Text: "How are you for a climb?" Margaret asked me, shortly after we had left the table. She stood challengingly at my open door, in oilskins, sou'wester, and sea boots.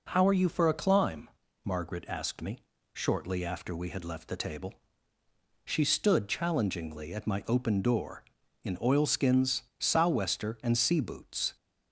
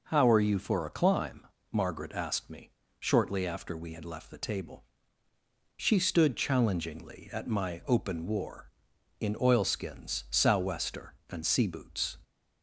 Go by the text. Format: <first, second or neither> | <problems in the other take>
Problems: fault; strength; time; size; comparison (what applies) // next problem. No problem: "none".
first | says "war" for "door"; at 8.2 s